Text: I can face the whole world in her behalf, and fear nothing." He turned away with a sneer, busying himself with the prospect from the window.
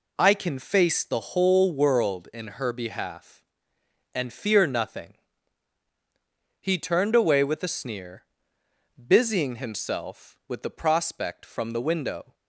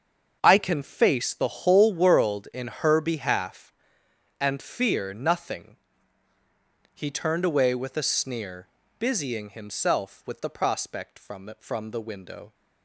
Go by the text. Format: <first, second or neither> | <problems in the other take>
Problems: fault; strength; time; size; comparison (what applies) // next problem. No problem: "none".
first | starts louder than the rest; until 1.4 s; 6.5 dB // says "from" twice; at 11.5 s